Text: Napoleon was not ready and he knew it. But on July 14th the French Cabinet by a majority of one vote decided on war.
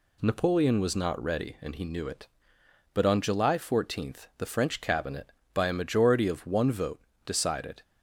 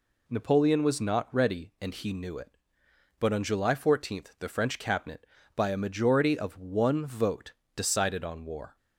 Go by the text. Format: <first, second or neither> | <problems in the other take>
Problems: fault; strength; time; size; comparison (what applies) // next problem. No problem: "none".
second | pauses between "vote" and "decided"; slight; at 6.9 s; 0.24 s long; slight in the second // stops before "on war"; at 7.8 s